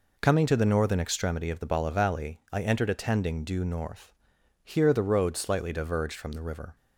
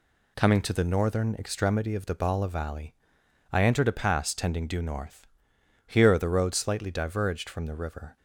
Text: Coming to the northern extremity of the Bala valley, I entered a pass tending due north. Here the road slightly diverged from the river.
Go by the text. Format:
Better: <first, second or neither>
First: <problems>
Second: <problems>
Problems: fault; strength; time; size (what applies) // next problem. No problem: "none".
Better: second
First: skips "pass"; at 2.9 s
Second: none